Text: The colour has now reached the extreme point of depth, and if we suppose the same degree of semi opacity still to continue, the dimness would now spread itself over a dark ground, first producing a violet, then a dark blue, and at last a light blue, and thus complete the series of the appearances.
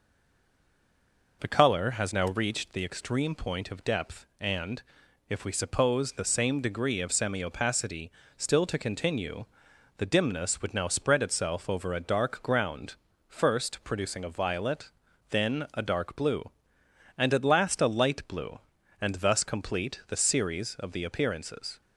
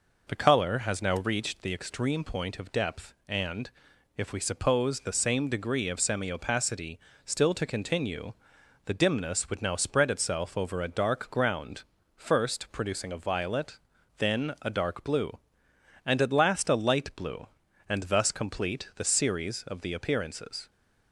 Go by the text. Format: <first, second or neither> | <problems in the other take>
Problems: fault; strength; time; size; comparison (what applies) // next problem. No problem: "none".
second | stays silent before the first word; noticeable; until 1.4 s; 1.4 s long // pauses between "and" and "if"; noticeable; at 4.8 s; 0.48 s long; noticeable in the second // pauses between "opacity" and "still"; slight; at 8.0 s; 0.28 s long; slight in the second